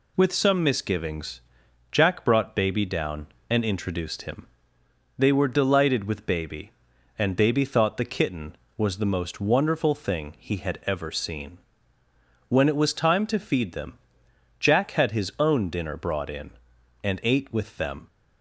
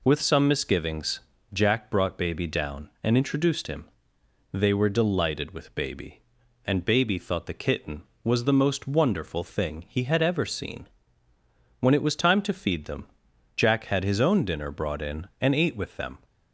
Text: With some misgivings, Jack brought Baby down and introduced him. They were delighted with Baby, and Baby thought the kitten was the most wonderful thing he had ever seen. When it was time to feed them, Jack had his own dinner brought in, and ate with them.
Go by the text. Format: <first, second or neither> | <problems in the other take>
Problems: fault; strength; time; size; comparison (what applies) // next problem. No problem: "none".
neither | none